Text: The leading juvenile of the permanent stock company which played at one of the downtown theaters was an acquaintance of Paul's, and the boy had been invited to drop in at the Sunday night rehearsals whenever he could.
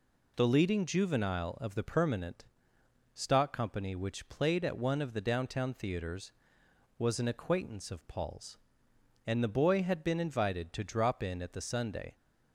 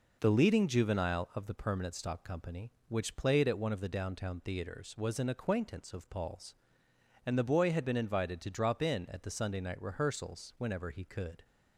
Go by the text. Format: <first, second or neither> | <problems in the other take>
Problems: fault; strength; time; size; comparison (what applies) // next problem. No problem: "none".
second | pauses between "permanent" and "stock"; noticeable; at 2.4 s; 0.70 s long // stops before "night rehearsals whenever he could"; at 12.1 s